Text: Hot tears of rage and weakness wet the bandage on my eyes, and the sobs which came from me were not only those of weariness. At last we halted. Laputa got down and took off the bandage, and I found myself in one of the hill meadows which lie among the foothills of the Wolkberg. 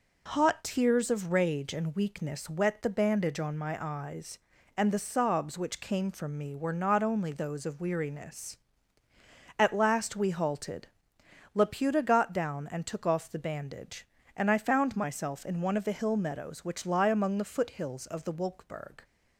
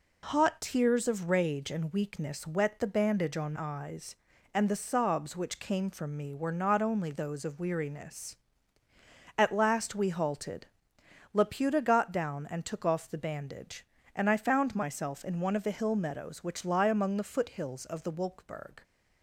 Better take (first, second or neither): first